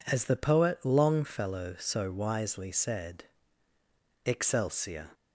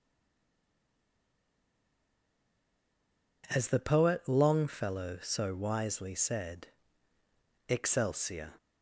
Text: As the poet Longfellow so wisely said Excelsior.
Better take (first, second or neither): first